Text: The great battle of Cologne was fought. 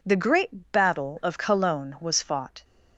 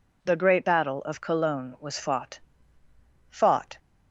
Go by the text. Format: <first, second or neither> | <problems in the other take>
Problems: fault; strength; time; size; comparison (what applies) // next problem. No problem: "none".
first | says "fought" twice; at 3.3 s